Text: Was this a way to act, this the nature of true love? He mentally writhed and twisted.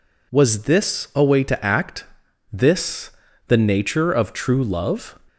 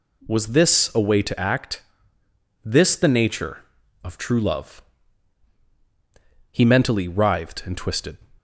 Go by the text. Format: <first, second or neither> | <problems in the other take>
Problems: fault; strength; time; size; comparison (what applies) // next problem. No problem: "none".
second | pauses between "this" and "the"; slight; at 3.1 s; 0.36 s long // stops before "He mentally writhed and twisted"; at 5.2 s